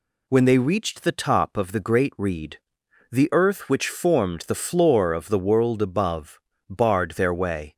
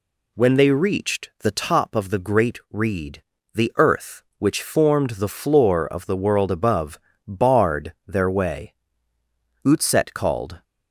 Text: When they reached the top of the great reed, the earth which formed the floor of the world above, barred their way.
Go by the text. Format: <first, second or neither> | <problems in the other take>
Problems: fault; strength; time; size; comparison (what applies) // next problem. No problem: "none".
first | goes on to say "Utset called"; noticeable; from 9.6 s on; 0.98 s long